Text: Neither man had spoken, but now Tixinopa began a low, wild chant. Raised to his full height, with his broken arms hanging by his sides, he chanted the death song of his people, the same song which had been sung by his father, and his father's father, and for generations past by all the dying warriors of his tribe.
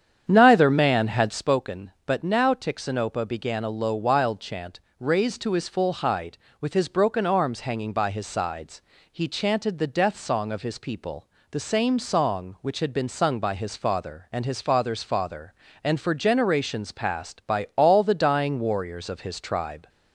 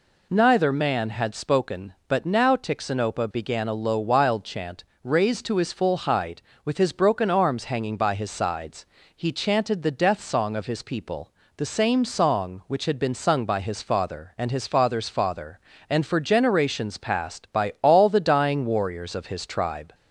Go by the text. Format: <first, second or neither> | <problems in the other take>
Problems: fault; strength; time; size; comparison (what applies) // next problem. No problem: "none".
second | starts louder than the rest; strong; until 1.6 s; 8.5 dB